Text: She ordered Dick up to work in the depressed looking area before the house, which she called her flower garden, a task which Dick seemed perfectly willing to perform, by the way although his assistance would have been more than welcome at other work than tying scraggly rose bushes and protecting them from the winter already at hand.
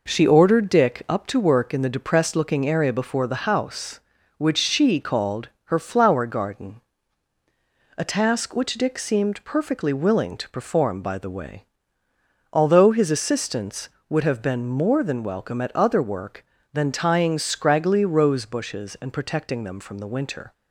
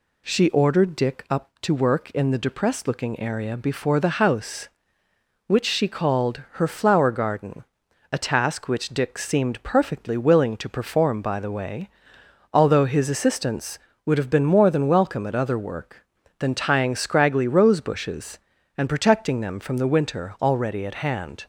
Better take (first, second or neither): second